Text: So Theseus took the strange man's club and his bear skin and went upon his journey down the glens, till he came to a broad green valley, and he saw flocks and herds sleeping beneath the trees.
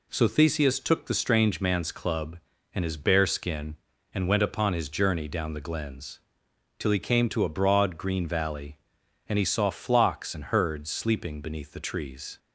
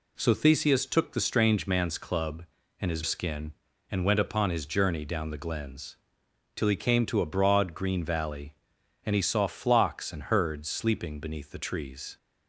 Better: first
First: none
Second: skips "bear"; at 3.0 s

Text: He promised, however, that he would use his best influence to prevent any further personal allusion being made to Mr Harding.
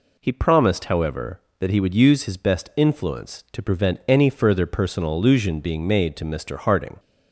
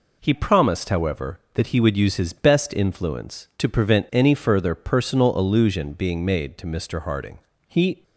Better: first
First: none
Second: goes on to say "He"; slight; from 7.6 s on; 0.36 s long

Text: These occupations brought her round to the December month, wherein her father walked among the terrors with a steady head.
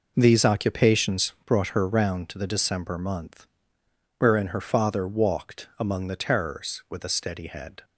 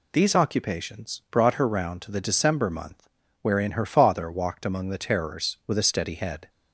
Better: neither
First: none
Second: none

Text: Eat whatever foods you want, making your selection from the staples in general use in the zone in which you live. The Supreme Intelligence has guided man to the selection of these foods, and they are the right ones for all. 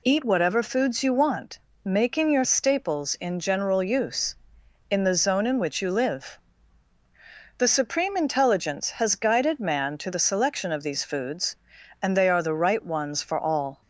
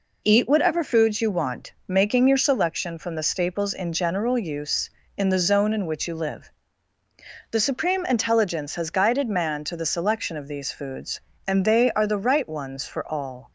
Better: second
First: skips "selection from the"; at 2.4 s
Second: none

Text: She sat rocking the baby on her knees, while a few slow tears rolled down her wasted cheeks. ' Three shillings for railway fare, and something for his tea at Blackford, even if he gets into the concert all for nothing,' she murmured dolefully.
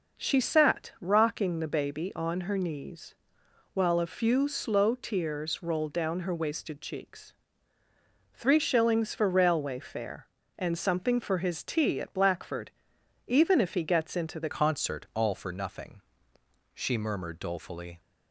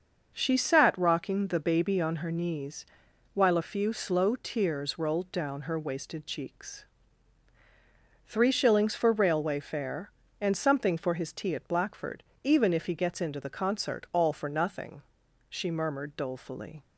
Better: second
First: starts louder than the rest; until 1.2 s; 6.5 dB // changes voice at "concert"; from 14.5 s on; 3.4 s long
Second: starts louder than the rest; until 1.3 s; 6.5 dB

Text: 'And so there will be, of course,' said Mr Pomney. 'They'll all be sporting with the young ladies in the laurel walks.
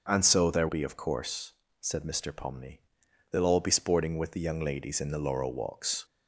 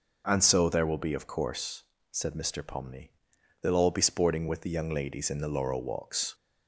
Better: second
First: skips "will"; at 0.6 s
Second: none

